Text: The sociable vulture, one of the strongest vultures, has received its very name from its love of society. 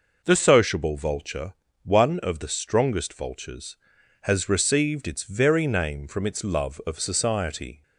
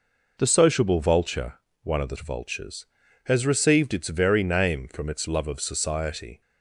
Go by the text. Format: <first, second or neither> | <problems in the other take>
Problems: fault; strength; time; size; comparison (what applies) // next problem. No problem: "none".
first | skips "strongest"; at 2.1 s